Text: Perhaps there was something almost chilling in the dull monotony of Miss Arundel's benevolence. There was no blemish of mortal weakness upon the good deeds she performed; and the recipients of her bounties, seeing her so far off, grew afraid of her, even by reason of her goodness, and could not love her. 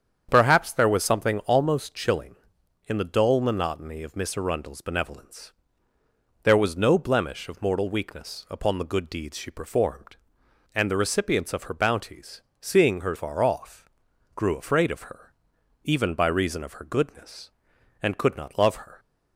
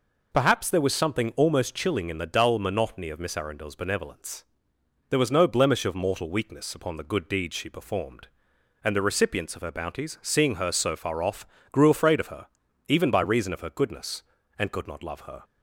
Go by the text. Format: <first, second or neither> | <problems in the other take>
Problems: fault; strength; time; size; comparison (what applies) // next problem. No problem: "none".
second | starts louder than the rest; strong; until 1.3 s; 8 dB // skips "so"; at 13.1 s